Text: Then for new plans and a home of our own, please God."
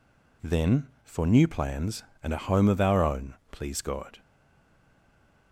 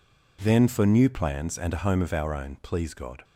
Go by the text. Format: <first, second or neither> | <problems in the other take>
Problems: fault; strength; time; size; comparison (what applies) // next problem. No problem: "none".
second | stays silent after the last word; noticeable; from 4.1 s on; 1.4 s long